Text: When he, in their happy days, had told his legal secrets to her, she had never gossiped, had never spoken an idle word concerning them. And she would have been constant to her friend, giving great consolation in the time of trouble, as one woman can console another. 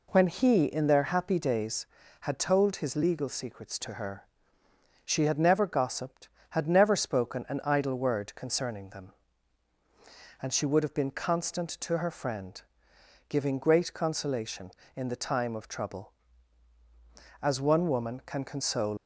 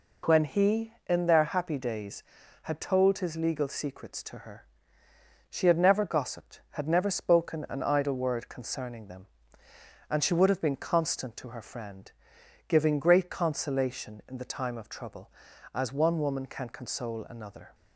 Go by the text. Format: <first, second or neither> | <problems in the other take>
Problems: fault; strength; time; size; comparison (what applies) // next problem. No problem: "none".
second | stops before "another"; at 18.9 s